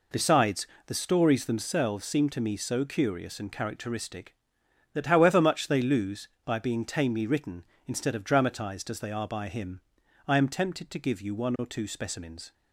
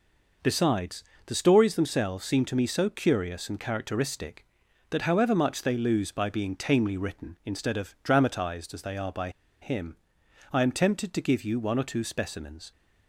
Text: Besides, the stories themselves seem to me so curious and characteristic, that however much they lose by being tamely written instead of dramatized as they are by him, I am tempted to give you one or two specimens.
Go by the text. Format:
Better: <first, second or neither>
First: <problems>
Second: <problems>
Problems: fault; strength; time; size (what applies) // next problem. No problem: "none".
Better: first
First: none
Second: pauses between "by" and "him"; slight; at 9.2 s; 0.31 s long